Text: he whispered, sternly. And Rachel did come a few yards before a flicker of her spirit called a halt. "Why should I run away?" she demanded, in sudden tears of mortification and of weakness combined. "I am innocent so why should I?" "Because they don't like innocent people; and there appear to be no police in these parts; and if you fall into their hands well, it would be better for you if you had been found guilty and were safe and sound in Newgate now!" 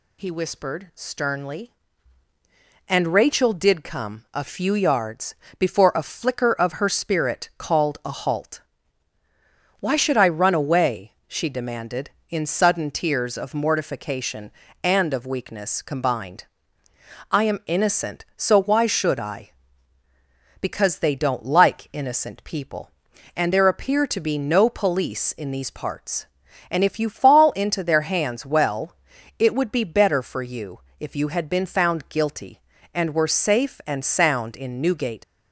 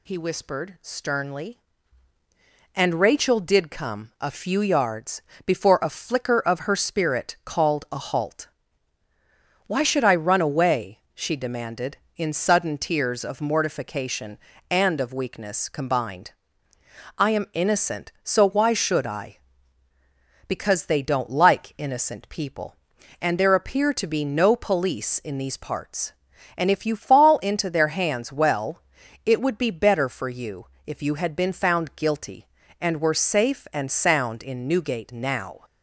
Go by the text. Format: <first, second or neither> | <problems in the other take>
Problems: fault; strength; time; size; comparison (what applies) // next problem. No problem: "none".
second | pauses between "yards" and "before"; slight; at 5.3 s; 0.24 s long; slight in the second // pauses between "you" and "if"; slight; at 30.7 s; 0.20 s long; slight in the second // stops before "now"; at 35.2 s